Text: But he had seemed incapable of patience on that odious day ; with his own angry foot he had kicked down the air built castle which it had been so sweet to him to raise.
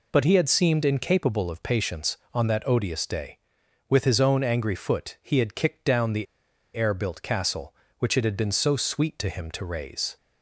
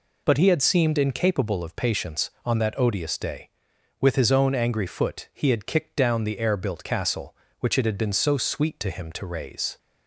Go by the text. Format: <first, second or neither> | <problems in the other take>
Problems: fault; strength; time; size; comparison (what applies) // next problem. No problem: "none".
second | pauses between "the" and "air"; noticeable; at 6.2 s; 0.49 s long